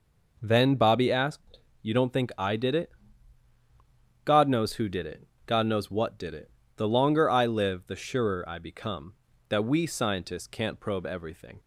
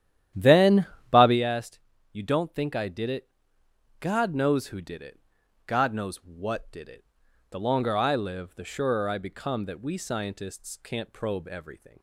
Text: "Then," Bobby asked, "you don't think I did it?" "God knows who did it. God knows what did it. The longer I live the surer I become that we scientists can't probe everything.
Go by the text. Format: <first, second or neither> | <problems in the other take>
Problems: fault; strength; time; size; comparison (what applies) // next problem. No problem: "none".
first | starts louder than the rest; strong; until 1.4 s; 11 dB